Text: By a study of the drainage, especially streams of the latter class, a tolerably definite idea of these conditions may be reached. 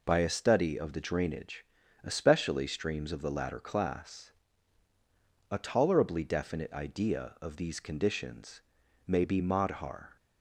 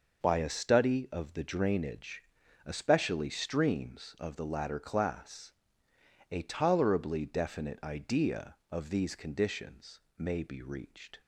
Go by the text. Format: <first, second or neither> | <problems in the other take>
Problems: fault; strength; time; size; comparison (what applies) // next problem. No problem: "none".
second | pauses between "conditions" and "may"; noticeable; at 8.5 s; 0.48 s long; slight in the second // says "madhar" for "reached"; at 9.3 s